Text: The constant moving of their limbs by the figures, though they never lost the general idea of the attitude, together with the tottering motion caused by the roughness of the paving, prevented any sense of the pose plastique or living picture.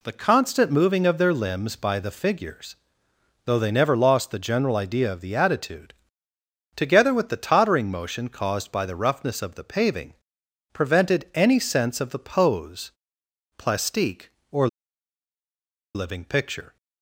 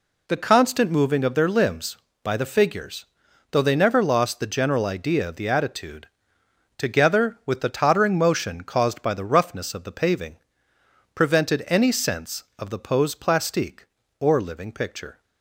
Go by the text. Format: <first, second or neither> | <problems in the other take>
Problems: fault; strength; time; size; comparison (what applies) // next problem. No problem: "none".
second | pauses between "pose" and "plastique"; noticeable; at 12.9 s; 0.68 s long // pauses between "or" and "living"; strong; at 14.6 s; 1.2 s long